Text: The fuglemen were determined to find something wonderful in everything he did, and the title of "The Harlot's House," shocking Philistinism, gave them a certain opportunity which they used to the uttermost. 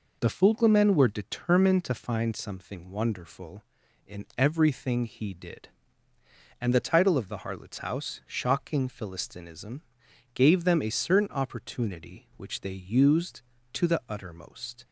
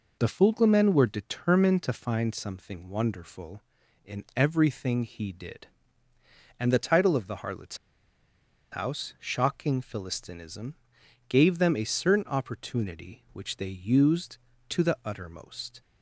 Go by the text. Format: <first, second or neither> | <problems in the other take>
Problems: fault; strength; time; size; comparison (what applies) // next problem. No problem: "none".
first | pauses between "Harlot's" and "House"; noticeable; at 7.7 s; 0.95 s long